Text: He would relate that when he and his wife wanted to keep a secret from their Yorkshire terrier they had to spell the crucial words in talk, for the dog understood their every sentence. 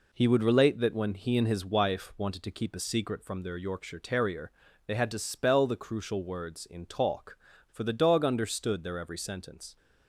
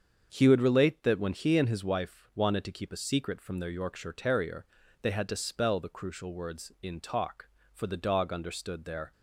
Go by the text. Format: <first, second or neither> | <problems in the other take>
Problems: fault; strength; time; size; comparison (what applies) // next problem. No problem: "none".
first | starts louder than the rest; strong; until 1.3 s; 7 dB // pauses between "terrier" and "they"; slight; at 4.6 s; 0.36 s long; slight in the first // stops before "every sentence"; at 9.1 s